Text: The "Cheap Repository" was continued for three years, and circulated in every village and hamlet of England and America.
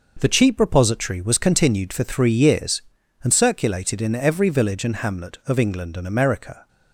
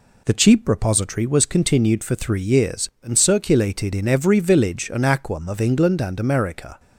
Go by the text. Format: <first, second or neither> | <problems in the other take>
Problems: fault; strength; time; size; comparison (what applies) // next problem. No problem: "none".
first | says "aquam" for "hamlet"; at 5.0 s